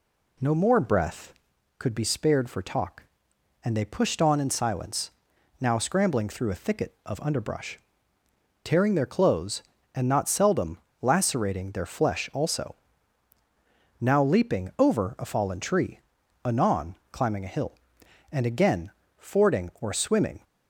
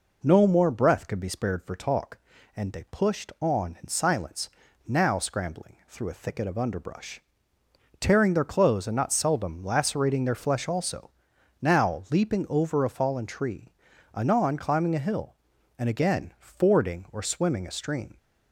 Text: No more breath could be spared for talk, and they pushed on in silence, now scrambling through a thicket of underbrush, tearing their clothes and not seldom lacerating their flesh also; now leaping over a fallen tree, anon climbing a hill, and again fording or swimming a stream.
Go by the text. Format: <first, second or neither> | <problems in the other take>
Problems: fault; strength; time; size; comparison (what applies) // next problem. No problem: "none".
second | pauses between "seldom" and "lacerating"; slight; at 10.7 s; 0.24 s long // pauses between "anon" and "climbing"; slight; at 16.9 s; 0.16 s long // pauses between "again" and "fording"; slight; at 18.9 s; 0.26 s long // stops before "a stream"; at 20.4 s